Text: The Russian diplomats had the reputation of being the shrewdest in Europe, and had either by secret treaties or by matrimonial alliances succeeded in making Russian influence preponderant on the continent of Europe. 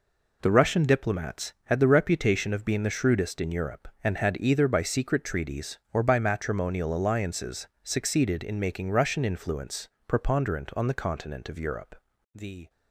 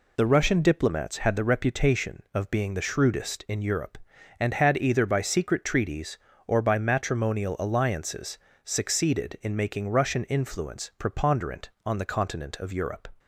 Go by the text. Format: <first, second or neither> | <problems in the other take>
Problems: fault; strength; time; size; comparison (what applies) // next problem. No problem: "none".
second | pauses between "alliances" and "succeeded"; slight; at 7.6 s; 0.16 s long; slight in the second // pauses between "influence" and "preponderant"; slight; at 9.8 s; 0.18 s long // goes on to say "The"; slight; from 12.3 s on; 0.36 s long